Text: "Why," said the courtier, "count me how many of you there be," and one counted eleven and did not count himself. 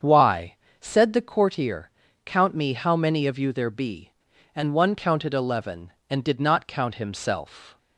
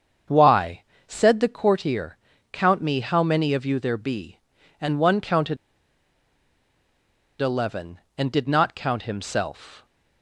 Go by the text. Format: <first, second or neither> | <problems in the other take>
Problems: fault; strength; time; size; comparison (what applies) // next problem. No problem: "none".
first | starts louder than the rest; strong; until 1.5 s; 7 dB; strong in the first // pauses between "counted" and "eleven"; strong; at 5.5 s; 1.8 s long